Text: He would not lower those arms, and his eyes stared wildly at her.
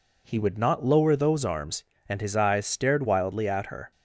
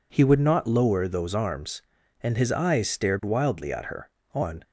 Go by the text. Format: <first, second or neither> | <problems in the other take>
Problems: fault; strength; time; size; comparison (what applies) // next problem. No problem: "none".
first | goes on to say "On"; slight; from 4.3 s on; 0.28 s long